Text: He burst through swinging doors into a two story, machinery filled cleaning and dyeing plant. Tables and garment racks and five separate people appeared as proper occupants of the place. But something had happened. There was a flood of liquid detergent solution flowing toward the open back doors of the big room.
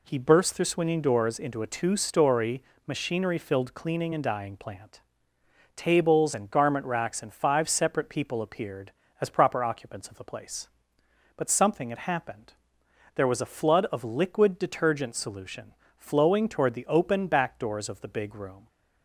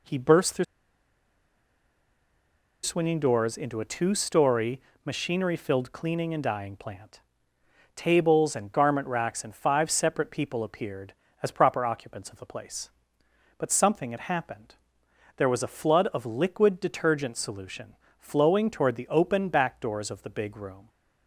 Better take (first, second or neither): first